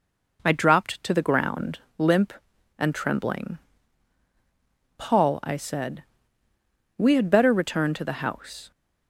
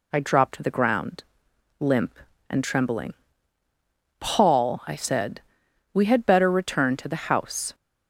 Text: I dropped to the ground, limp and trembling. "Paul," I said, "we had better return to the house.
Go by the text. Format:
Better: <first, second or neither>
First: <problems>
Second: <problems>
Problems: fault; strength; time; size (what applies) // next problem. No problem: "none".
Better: neither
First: none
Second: none